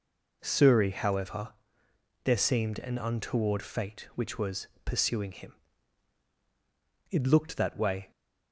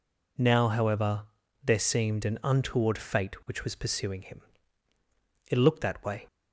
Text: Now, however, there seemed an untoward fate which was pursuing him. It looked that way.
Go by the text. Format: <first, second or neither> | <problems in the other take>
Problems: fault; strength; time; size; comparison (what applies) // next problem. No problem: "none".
second | says "Suri" for "Now"; at 0.4 s // pauses between "was" and "pursuing"; slight; at 4.6 s; 0.18 s long